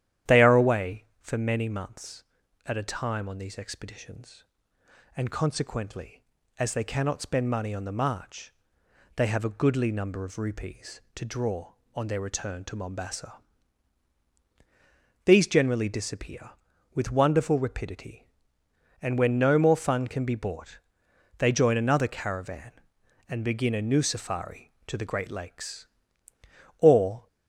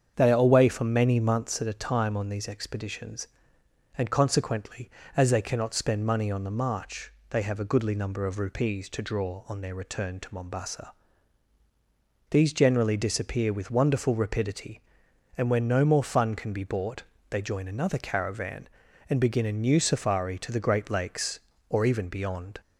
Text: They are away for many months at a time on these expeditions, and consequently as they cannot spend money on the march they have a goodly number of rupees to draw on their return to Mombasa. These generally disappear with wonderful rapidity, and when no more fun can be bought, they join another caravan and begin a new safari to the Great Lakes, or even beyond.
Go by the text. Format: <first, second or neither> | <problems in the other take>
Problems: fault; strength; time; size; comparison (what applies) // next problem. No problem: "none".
second | starts louder than the rest; strong; until 1.4 s; 11 dB; strong in the second // pauses between "march" and "they"; noticeable; at 8.5 s; 0.62 s long; slight in the second // stops before "even beyond"; at 27.2 s